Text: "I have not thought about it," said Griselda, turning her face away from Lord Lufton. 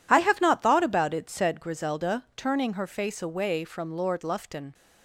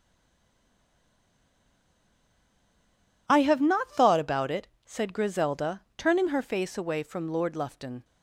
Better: first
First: none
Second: stays silent before the first word; strong; until 3.2 s; 3.2 s long

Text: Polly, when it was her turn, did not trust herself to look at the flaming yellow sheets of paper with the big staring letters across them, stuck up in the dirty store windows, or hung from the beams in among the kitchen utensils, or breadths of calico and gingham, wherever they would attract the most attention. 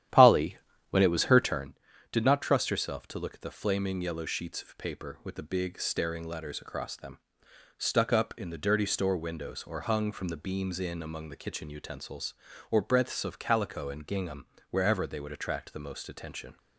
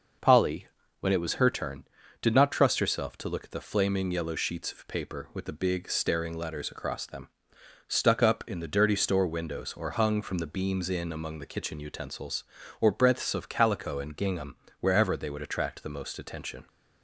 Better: second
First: starts louder than the rest; strong; until 1.7 s; 11.5 dB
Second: none

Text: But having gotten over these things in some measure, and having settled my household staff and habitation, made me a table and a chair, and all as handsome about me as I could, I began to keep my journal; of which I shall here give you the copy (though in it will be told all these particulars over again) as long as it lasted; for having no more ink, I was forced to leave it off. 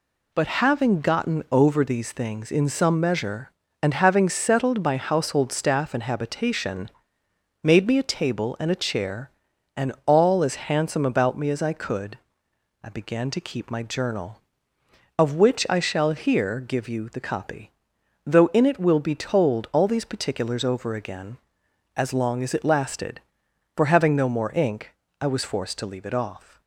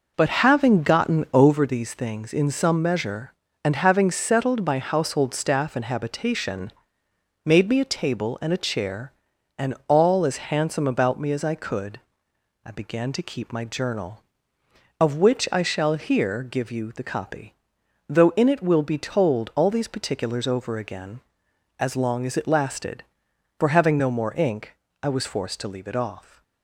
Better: first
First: none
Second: starts louder than the rest; noticeable; until 1.6 s; 5.5 dB

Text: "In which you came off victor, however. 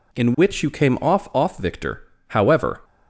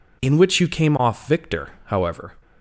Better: second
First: says "off" twice; at 1.3 s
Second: none

